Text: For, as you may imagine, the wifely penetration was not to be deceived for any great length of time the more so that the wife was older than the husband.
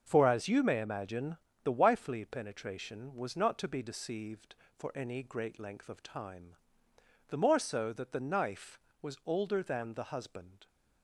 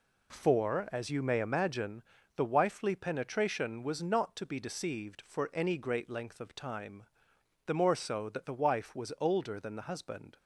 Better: second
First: starts louder than the rest; until 1.0 s; 6.5 dB // pauses between "time" and "the"; noticeable; at 6.5 s; 0.72 s long // says "knife" for "wife"; at 8.2 s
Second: pauses between "time" and "the"; noticeable; at 7.0 s; 0.62 s long

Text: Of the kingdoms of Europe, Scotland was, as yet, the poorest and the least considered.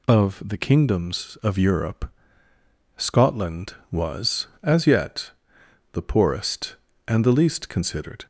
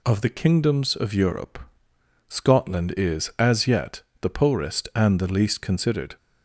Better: first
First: none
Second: says "is" for "was"; at 2.9 s

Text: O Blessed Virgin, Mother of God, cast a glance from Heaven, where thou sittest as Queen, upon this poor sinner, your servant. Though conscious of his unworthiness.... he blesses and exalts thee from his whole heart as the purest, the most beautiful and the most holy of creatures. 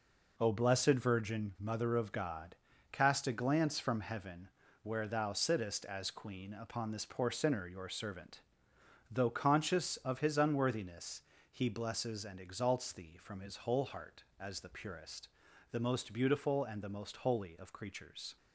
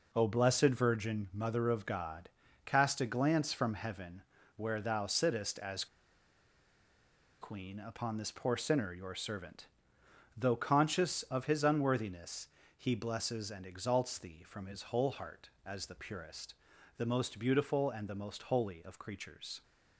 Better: first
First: none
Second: pauses between "as" and "Queen"; strong; at 5.8 s; 1.5 s long

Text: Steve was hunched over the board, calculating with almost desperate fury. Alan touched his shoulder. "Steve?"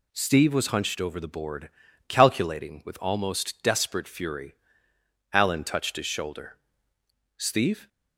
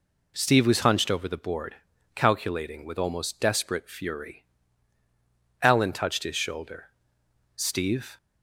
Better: neither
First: none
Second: none

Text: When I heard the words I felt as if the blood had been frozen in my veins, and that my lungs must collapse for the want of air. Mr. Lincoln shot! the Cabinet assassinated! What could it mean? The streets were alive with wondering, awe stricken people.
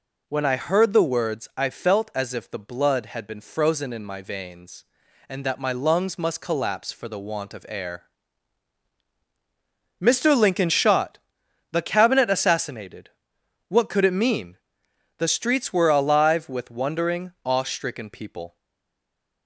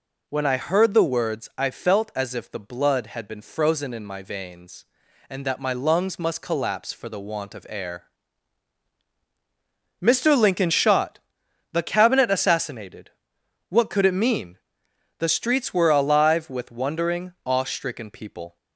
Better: second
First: stays silent after the last word; slight; from 18.5 s on; 0.9 s long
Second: none

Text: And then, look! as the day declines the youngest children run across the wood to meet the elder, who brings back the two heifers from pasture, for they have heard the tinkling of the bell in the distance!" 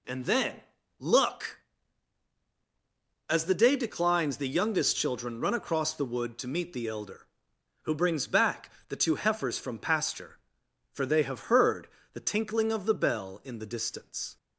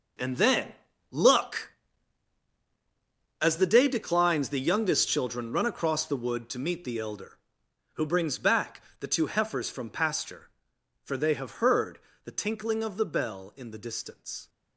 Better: first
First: pauses between "back" and "the"; slight; at 8.6 s; 0.18 s long // pauses between "heard" and "the"; slight; at 11.8 s; 0.26 s long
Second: gets quieter; strong; throughout; 13.5 dB // pauses between "back" and "the"; slight; at 8.8 s; 0.18 s long // pauses between "heard" and "the"; slight; at 11.9 s; 0.26 s long

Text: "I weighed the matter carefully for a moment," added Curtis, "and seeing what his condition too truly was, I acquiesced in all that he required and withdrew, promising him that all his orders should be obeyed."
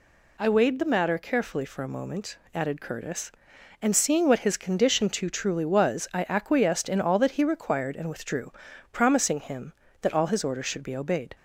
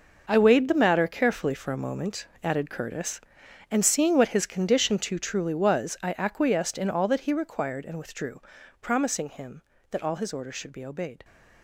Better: first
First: none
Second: gets quieter; strong; throughout; 12.5 dB

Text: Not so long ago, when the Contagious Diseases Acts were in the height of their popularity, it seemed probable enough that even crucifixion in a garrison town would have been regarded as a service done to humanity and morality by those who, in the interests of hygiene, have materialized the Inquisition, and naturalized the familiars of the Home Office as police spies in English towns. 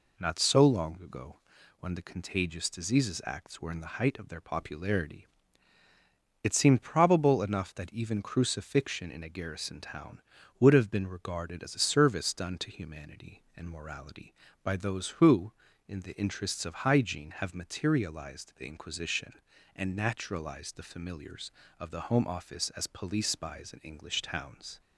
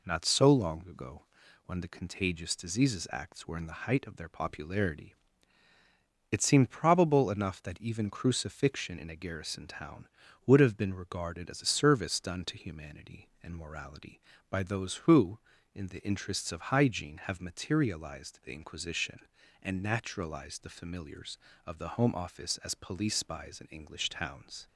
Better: neither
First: none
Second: none

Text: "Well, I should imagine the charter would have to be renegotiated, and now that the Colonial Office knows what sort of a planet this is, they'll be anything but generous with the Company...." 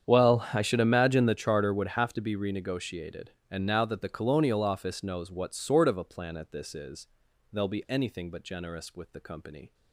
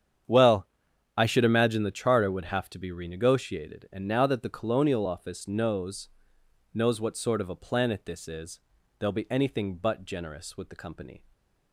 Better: first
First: starts louder than the rest; strong; until 1.1 s; 8.5 dB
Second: starts louder than the rest; strong; until 1.7 s; 8.5 dB // says "knows" twice; at 6.7 s

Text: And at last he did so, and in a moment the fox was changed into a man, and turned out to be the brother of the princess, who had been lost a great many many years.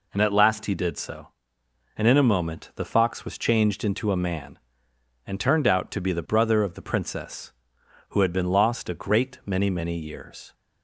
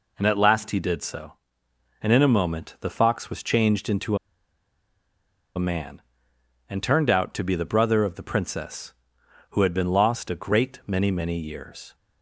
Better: first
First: none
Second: pauses between "into" and "a"; strong; at 4.1 s; 1.3 s long

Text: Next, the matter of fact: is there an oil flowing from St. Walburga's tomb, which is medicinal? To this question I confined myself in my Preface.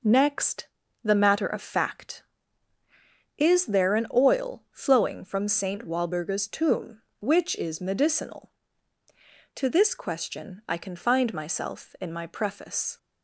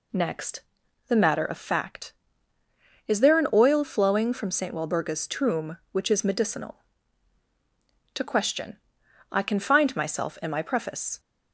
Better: first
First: none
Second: skips "this"; at 8.2 s // pauses between "question" and "I"; noticeable; at 8.7 s; 0.52 s long

